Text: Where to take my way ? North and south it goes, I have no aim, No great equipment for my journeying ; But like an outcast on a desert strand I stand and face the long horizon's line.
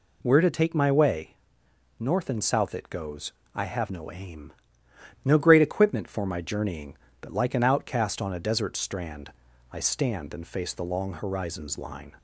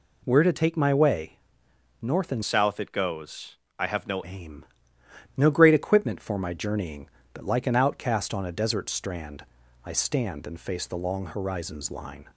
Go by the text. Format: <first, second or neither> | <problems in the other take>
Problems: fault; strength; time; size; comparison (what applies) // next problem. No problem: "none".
first | changes voice from "south" to "no"; from 2.4 to 4.2 s; 1.8 s long // pauses between "strand" and "I"; at 9.4 s; 0.40 s long; also in the first